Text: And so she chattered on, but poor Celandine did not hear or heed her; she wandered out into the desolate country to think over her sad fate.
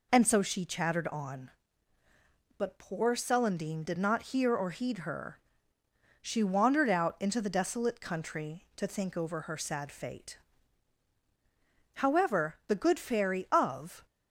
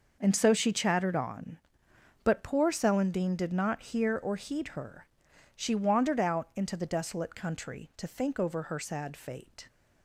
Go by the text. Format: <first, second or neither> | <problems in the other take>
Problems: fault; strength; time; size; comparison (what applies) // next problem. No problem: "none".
second | goes on to say "However the good Fairy of"; strong; from 11.9 s on; 2.1 s long